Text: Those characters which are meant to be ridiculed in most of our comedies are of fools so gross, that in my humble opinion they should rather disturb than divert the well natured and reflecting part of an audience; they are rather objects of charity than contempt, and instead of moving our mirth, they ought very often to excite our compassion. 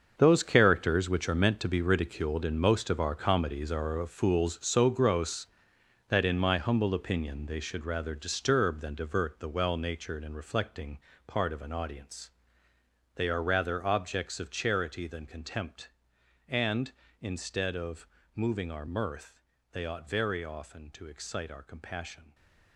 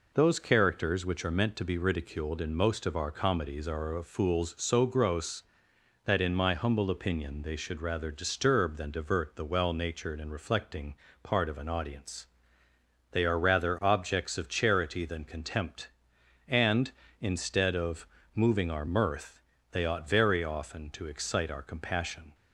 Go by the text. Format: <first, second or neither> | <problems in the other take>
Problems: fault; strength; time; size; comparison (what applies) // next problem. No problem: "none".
second | gets quieter; strong; throughout; 12.5 dB // pauses between "reflecting" and "part"; slight; at 10.9 s; 0.28 s long; slight in the second // pauses between "of" and "moving"; slight; at 18.0 s; 0.28 s long; slight in the second